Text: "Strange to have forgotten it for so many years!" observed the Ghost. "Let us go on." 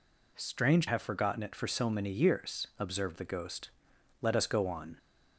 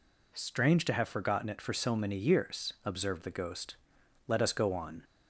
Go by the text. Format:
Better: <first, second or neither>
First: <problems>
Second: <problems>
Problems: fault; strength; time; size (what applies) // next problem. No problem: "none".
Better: second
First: skips "to"; at 0.8 s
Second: none